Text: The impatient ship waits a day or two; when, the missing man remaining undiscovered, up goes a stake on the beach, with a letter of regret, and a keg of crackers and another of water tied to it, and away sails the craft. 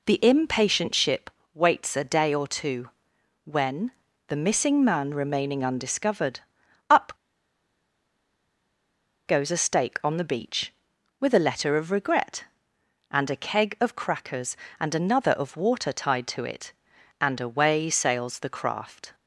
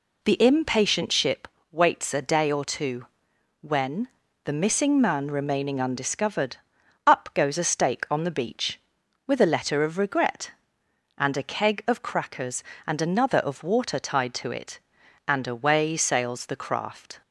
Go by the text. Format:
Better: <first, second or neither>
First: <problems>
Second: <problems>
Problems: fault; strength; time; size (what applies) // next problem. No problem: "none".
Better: second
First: pauses between "ship" and "waits"; slight; at 1.3 s; 0.24 s long // pauses between "up" and "goes"; strong; at 7.1 s; 2.1 s long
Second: pauses between "ship" and "waits"; slight; at 1.4 s; 0.24 s long